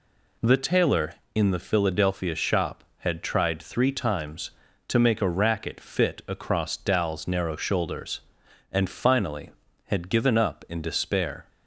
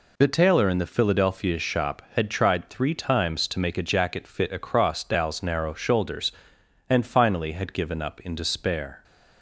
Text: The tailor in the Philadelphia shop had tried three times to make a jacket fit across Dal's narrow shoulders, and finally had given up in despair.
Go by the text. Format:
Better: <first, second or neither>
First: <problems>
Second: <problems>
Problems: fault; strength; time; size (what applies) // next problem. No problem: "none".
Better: second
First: says "racket" for "jacket"; at 5.2 s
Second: none